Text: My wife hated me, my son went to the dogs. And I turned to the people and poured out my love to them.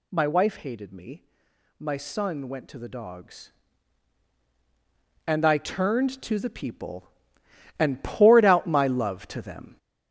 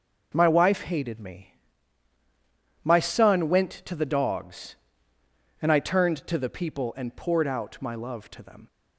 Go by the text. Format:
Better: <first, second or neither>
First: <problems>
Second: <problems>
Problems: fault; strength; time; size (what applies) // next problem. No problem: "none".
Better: second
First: gets louder; noticeable; throughout; 5 dB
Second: none